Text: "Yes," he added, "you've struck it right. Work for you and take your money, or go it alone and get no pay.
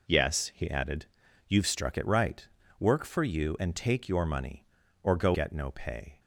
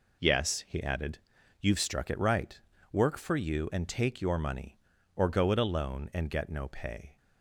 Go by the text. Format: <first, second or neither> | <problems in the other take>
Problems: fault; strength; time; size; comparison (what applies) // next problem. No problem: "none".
second | skips "it alone and"; at 5.3 s